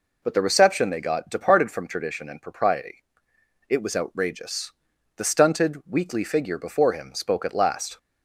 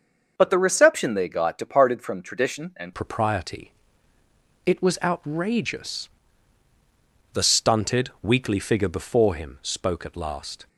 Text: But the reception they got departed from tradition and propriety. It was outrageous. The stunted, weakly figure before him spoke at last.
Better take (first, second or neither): first